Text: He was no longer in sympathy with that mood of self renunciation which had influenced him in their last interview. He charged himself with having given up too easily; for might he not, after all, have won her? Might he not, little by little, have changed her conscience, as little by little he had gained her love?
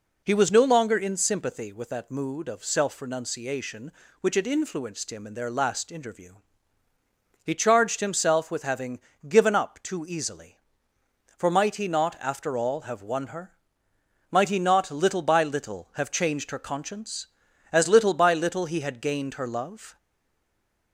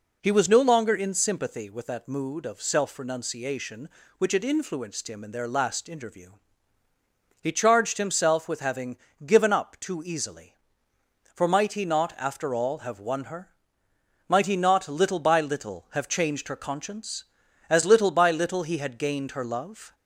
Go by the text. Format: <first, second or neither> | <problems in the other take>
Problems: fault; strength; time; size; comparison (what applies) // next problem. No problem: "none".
second | pauses between "having" and "given"; slight; at 9.0 s; 0.26 s long; slight in the second // stays silent after the last word; from 19.9 s on; 1.0 s long